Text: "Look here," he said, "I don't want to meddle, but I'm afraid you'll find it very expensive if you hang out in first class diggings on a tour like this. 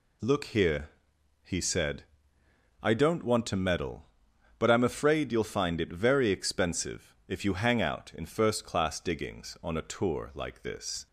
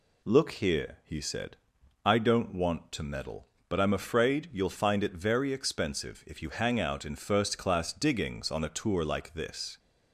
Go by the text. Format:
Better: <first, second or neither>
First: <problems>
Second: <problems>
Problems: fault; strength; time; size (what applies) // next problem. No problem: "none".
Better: neither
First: none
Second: none